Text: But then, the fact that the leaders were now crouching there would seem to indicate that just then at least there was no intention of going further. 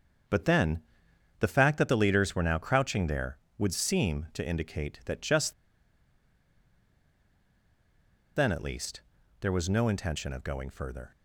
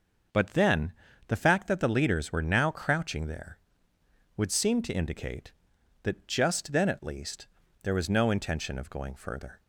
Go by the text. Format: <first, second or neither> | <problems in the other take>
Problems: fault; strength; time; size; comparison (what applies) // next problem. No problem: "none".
second | starts louder than the rest; until 1.8 s; 7 dB; also in the second // pauses between "just" and "then"; strong; at 5.5 s; 2.8 s long // pauses between "least" and "there"; at 9.0 s; 0.40 s long; slight in the second